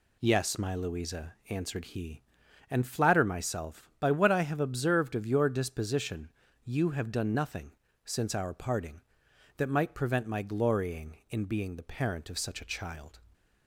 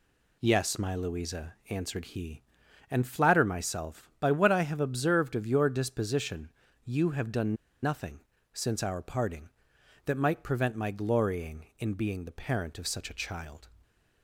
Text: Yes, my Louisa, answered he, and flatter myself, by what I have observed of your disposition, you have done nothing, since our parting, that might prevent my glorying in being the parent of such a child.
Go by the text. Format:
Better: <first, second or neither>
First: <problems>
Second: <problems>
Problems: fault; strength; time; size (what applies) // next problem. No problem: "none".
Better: first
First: none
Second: pauses between "done" and "nothing"; slight; at 7.5 s; 0.26 s long